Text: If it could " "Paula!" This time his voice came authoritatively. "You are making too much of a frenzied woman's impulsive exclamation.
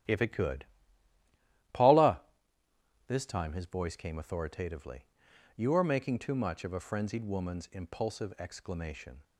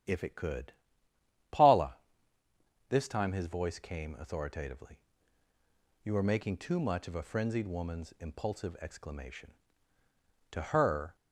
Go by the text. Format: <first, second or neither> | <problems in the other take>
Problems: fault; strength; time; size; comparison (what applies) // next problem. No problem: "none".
first | goes on to say "To her"; noticeable; from 10.4 s on; 0.66 s long